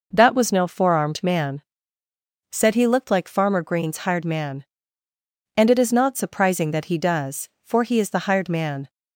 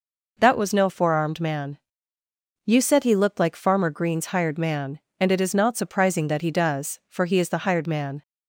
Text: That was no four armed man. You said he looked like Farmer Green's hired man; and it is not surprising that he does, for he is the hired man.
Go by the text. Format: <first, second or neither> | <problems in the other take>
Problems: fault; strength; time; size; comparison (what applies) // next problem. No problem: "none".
second | skips "You"; at 2.0 s